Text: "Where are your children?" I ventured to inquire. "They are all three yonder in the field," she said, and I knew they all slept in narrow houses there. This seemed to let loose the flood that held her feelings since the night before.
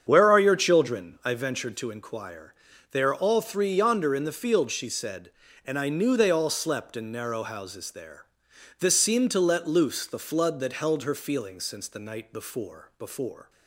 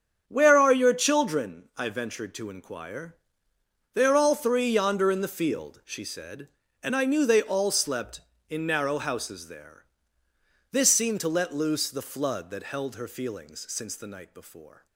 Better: second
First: starts louder than the rest; strong; until 1.0 s; 7.5 dB // says "before" twice; at 12.9 s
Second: starts louder than the rest; strong; until 1.2 s; 7.5 dB

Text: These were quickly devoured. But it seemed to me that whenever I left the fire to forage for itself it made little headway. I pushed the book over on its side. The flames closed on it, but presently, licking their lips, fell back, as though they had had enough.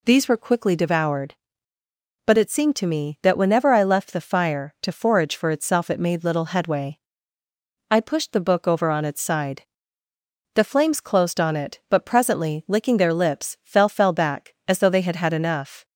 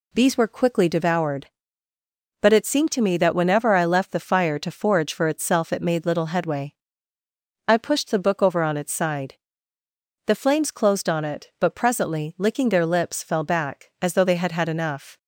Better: second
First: says "fell" twice; at 13.8 s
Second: none

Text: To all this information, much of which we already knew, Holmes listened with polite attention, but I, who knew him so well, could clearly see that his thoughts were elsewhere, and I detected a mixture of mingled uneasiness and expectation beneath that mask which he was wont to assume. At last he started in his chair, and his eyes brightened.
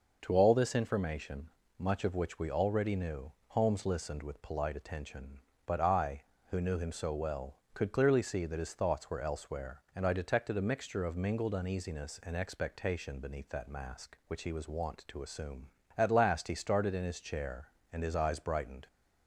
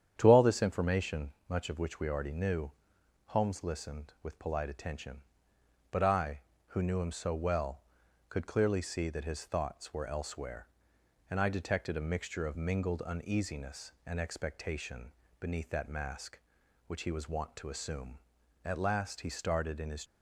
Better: first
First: none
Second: starts louder than the rest; strong; until 1.1 s; 9 dB // pauses between "expectation" and "beneath"; slight; at 15.1 s; 0.28 s long // stops before "chair and his eyes brightened"; at 20.0 s

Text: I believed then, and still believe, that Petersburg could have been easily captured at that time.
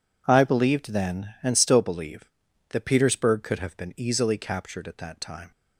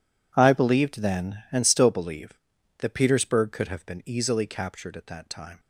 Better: first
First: none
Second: gets quieter; strong; throughout; 16 dB

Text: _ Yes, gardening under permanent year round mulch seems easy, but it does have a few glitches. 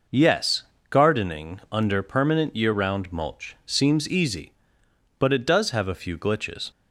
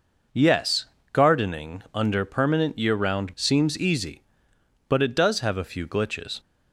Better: first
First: none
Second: skips "mulch"; at 3.3 s

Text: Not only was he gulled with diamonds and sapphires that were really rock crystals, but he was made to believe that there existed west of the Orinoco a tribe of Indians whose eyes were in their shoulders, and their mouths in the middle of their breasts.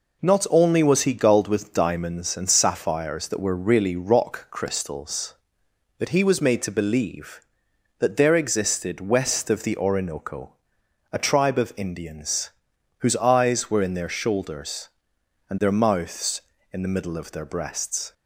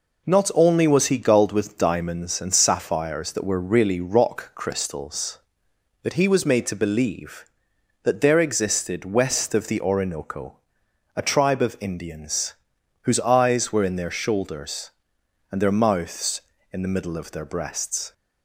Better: neither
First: pauses between "Orinoco" and "a"; noticeable; at 10.5 s; 0.60 s long // pauses between "Indians" and "whose"; noticeable; at 12.4 s; 0.50 s long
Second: pauses between "Orinoco" and "a"; noticeable; at 10.5 s; 0.60 s long // pauses between "Indians" and "whose"; noticeable; at 12.5 s; 0.50 s long

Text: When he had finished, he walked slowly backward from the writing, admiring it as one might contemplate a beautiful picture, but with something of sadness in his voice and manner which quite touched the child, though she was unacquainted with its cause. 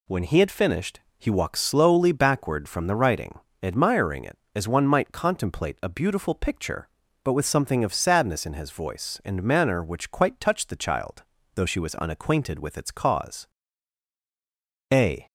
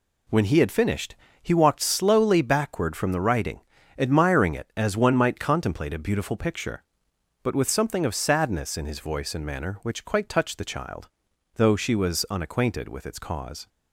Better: second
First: goes on to say "A"; slight; from 14.9 s on; 0.34 s long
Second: none

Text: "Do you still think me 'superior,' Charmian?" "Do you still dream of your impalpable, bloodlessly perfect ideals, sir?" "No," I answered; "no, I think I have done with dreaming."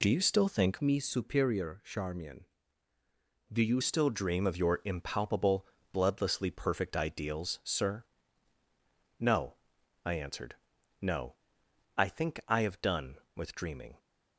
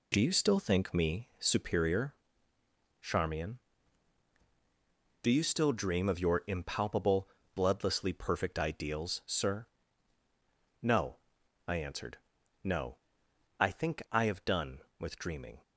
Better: second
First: changes voice from "me" to "you"; from 0.8 to 3.8 s; 3.0 s long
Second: none

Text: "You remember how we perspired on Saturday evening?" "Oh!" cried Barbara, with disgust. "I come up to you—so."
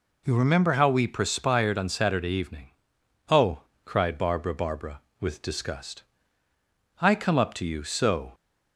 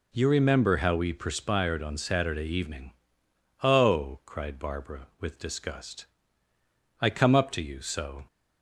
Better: second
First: says "Barbara" twice; at 4.5 s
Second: none

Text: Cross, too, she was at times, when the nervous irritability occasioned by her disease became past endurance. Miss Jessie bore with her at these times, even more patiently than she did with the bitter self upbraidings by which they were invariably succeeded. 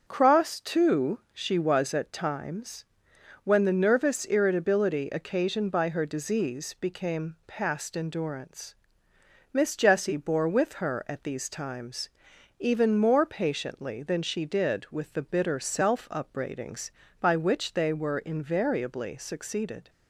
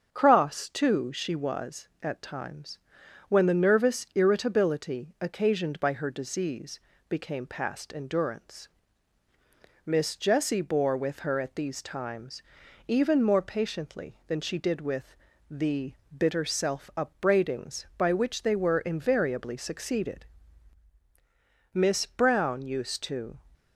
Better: first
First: starts louder than the rest; until 1.0 s; 6.5 dB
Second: starts louder than the rest; until 1.1 s; 7 dB // pauses between "disease" and "became"; slight; at 6.8 s; 0.28 s long // pauses between "with" and "the"; slight; at 15.1 s; 0.34 s long // pauses between "the" and "bitter"; slight; at 15.9 s; 0.22 s long // goes on to say "Miss Brown used to"; strong; from 21.7 s on; 1.6 s long

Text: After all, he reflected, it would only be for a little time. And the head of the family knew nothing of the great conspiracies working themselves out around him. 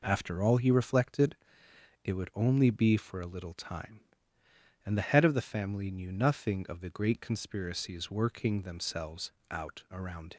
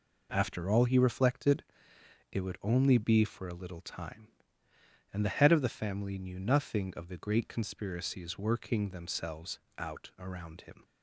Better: second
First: pauses between "themselves" and "out"; slight; at 9.3 s; 0.18 s long // stops before "him"; at 10.3 s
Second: pauses between "themselves" and "out"; slight; at 9.5 s; 0.18 s long

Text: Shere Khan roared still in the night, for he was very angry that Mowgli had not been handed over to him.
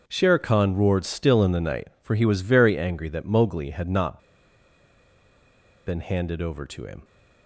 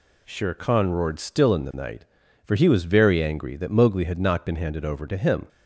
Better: second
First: starts louder than the rest; until 1.0 s; 6.5 dB // pauses between "not" and "been"; strong; at 4.1 s; 1.6 s long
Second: none

